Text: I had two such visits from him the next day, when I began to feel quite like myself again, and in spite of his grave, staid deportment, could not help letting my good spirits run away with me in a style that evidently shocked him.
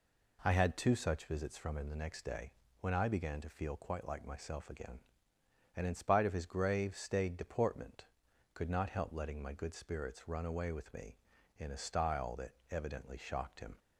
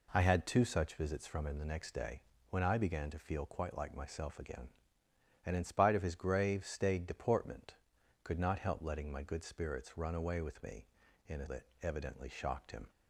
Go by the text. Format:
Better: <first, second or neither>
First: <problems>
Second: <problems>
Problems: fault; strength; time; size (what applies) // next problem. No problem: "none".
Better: first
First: pauses between "that" and "evidently"; slight; at 12.5 s; 0.16 s long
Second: skips "style"; at 11.4 s // pauses between "that" and "evidently"; slight; at 11.6 s; 0.16 s long